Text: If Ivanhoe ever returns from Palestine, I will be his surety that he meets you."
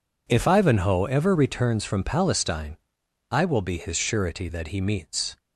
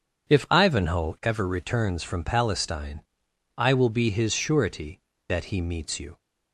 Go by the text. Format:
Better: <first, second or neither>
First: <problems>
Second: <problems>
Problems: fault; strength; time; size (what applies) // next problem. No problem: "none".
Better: second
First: stops before "you"; at 5.3 s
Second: none